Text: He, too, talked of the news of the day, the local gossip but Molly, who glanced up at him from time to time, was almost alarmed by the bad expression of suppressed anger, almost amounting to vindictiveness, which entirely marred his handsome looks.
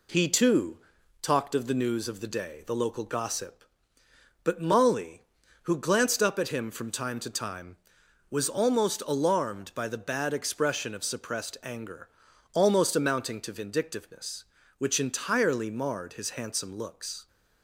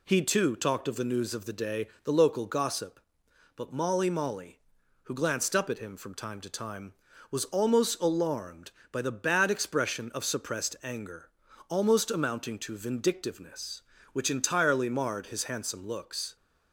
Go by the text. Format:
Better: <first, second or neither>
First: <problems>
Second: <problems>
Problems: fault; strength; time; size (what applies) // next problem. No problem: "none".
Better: first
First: none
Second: says "Molly" twice; at 4.1 s